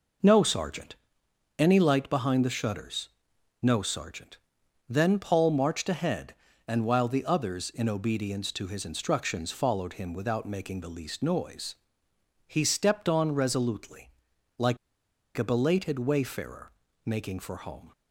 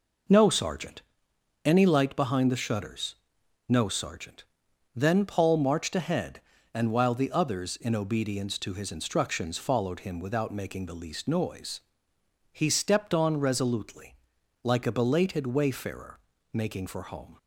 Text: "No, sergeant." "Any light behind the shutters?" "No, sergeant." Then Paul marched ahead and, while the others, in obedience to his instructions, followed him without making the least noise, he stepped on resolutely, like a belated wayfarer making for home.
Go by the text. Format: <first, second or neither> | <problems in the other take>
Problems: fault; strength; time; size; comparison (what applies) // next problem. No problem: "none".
second | pauses between "like" and "a"; noticeable; at 14.7 s; 0.60 s long // pauses between "wayfarer" and "making"; slight; at 16.7 s; 0.32 s long; slight in the second